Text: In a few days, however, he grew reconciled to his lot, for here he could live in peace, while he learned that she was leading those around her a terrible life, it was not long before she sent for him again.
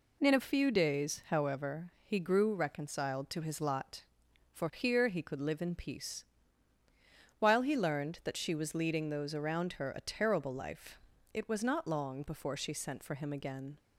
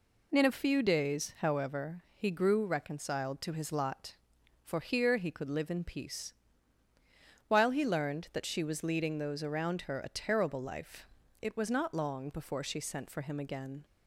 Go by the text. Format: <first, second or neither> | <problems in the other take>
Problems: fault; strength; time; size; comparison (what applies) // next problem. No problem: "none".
neither | none